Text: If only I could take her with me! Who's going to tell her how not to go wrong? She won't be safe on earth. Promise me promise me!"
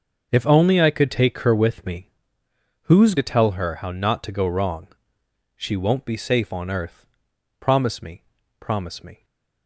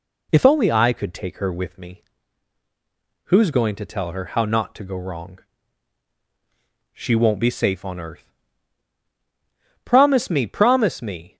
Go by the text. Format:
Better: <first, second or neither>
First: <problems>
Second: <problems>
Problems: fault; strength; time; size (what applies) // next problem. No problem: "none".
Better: second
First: starts louder than the rest; until 1.3 s; 6.5 dB // skips "going"; at 3.1 s // pauses between "me" and "promise"; at 8.2 s; 0.38 s long // stays silent after the last word; slight; from 9.1 s on; 0.5 s long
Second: none